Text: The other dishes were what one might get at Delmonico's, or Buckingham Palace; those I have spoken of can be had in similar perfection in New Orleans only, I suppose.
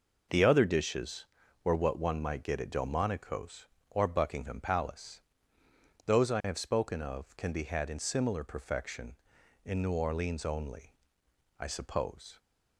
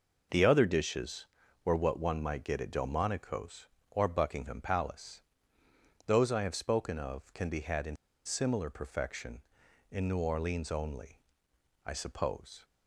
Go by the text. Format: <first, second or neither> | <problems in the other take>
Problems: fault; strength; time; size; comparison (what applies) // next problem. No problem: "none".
first | pauses between "in" and "similar"; slight; at 7.9 s; 0.30 s long